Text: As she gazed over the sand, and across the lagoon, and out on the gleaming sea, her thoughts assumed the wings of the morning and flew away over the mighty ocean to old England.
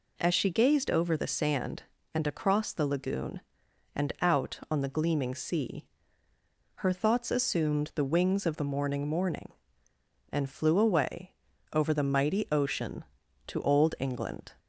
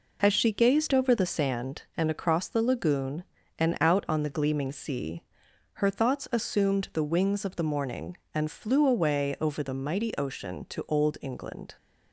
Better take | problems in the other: second | says "morning" twice; at 9.0 s // pauses between "away" and "over"; at 11.3 s; 0.40 s long

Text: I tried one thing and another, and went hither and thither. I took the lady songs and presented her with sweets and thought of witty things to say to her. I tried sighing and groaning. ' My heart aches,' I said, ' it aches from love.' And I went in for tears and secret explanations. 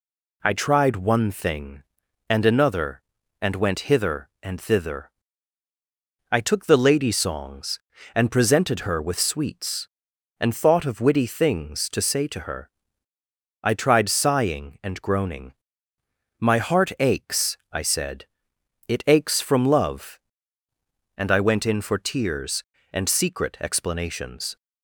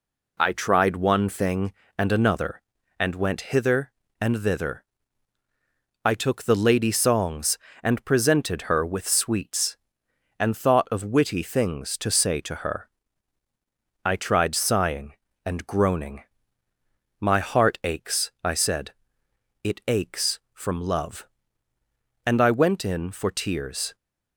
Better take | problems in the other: first | stops before "and secret explanations"; at 23.9 s

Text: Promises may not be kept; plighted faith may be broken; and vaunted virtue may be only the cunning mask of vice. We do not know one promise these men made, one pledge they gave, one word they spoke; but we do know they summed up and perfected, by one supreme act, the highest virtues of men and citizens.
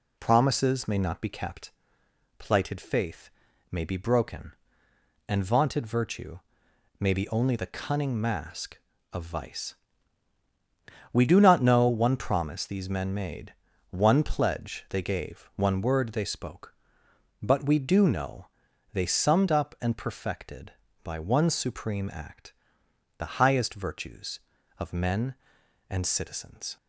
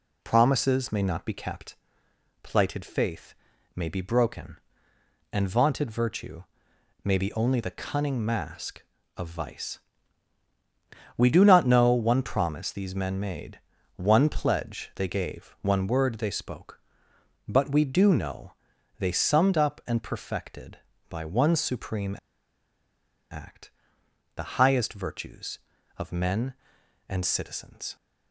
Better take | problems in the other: first | pauses between "faith" and "may"; at 3.3 s; 0.40 s long; also in the first // pauses between "virtue" and "may"; noticeable; at 6.4 s; 0.60 s long; noticeable in the first // pauses between "know" and "they"; noticeable; at 18.5 s; 0.46 s long; noticeable in the first // pauses between "supreme" and "act"; at 22.1 s; 1.1 s long

